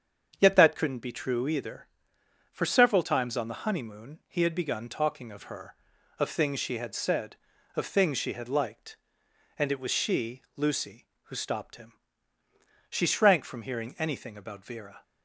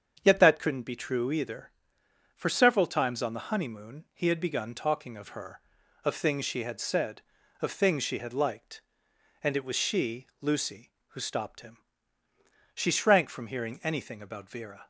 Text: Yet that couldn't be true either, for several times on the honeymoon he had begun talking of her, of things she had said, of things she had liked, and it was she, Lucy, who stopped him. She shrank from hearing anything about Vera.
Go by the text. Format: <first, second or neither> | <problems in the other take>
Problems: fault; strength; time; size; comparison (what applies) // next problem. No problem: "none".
neither | starts louder than the rest; strong; the same in both